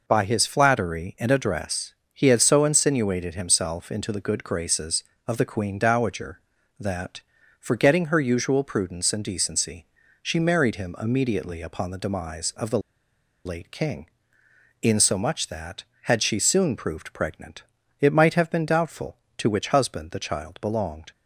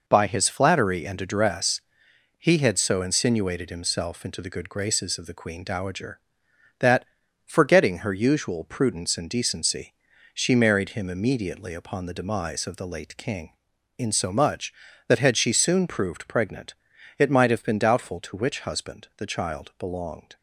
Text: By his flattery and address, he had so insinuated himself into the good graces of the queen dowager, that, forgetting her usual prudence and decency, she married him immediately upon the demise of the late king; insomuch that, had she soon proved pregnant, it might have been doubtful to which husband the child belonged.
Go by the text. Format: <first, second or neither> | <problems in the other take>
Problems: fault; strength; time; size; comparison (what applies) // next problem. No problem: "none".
second | pauses between "the" and "late"; noticeable; at 12.7 s; 0.66 s long